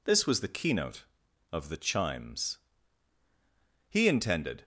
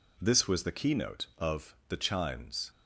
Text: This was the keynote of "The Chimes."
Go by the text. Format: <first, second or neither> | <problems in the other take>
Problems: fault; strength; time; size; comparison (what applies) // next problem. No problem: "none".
second | goes on to say "He intended"; noticeable; from 3.9 s on; 0.74 s long